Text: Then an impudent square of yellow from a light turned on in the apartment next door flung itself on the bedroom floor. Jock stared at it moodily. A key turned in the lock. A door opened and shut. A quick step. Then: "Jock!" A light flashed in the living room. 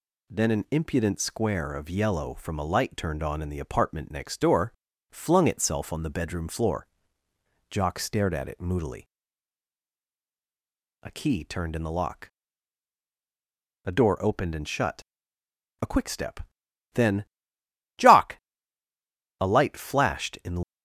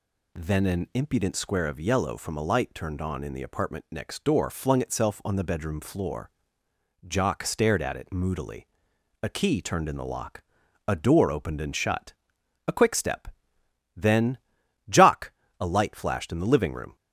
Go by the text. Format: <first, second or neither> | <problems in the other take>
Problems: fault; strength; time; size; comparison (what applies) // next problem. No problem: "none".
second | pauses between "door" and "flung"; at 4.7 s; 0.40 s long // stops before "living room"; at 20.6 s